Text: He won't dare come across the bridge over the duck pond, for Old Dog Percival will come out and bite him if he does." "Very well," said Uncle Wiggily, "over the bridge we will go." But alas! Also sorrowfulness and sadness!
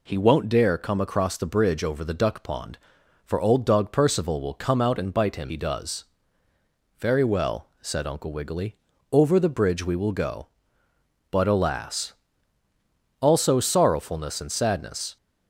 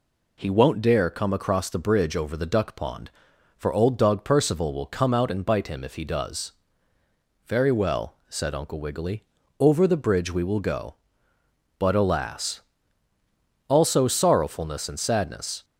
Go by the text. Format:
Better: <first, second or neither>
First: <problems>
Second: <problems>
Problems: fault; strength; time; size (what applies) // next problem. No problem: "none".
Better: second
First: skips "if"; at 5.4 s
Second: none